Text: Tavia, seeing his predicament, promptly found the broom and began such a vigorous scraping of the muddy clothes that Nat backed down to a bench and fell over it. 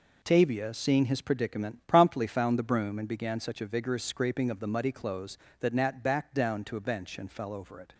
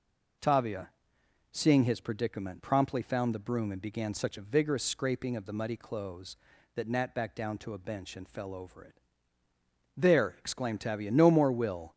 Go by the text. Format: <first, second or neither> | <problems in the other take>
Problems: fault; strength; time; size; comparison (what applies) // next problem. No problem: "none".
first | goes on to say "There exclaimed Tavia no more will"; strong; from 9.9 s on; 1.9 s long